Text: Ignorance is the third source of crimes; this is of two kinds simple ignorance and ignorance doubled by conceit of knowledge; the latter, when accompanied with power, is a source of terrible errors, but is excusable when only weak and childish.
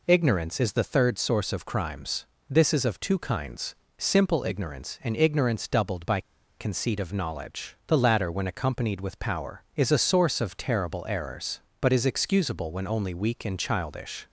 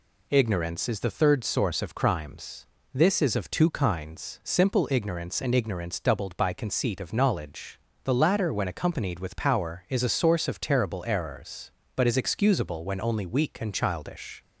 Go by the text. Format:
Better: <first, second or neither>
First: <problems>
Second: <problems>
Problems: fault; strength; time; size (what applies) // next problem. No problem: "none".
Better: second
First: pauses between "kinds" and "simple"; slight; at 3.7 s; 0.24 s long // pauses between "by" and "conceit"; at 6.1 s; 0.37 s long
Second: none